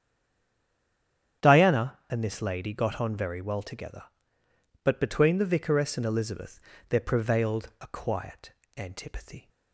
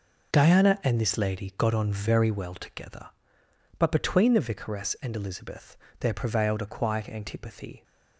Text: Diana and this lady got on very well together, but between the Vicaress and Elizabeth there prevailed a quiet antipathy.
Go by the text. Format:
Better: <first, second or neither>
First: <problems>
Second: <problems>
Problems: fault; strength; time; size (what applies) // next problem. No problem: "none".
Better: second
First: stays silent before the first word; noticeable; until 1.4 s; 1.4 s long // starts louder than the rest; strong; until 2.5 s; 9.5 dB // pauses between "Elizabeth" and "there"; slight; at 6.5 s; 0.30 s long // pauses between "quiet" and "antipathy"; slight; at 8.5 s; 0.24 s long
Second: pauses between "Elizabeth" and "there"; slight; at 5.7 s; 0.24 s long